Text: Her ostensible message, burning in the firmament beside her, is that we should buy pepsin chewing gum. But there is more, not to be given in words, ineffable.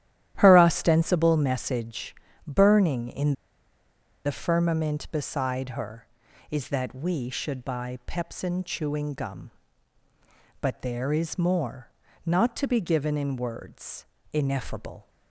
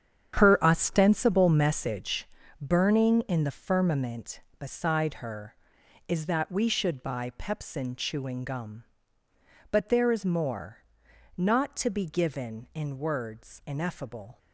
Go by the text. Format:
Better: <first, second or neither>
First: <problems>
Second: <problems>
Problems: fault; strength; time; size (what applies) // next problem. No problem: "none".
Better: second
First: starts louder than the rest; strong; until 1.4 s; 12 dB // pauses between "in" and "the"; noticeable; at 3.3 s; 0.93 s long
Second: starts louder than the rest; strong; until 1.4 s; 8.5 dB